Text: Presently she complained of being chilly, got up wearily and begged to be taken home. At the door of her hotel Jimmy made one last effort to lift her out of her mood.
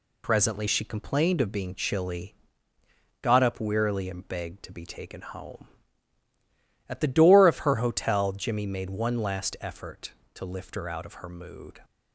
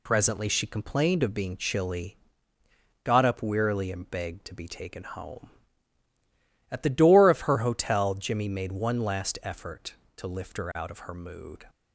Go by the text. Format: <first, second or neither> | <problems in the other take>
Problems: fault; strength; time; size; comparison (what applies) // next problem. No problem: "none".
neither | none